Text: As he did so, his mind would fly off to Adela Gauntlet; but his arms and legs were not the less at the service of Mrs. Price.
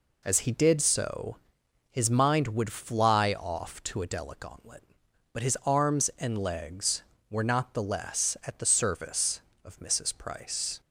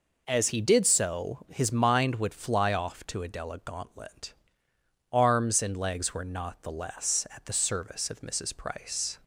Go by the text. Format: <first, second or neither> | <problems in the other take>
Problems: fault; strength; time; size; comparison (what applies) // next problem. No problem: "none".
first | skips "but his"; at 4.7 s